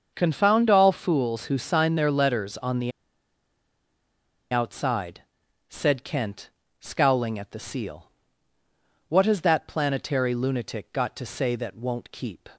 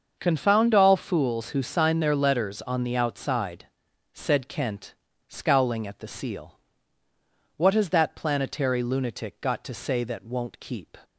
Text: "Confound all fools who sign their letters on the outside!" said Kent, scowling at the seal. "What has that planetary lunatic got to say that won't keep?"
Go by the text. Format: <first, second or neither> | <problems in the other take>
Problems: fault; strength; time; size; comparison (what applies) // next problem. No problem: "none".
second | starts louder than the rest; until 1.1 s; 6.5 dB; also in the second // pauses between "the" and "outside"; strong; at 2.9 s; 1.6 s long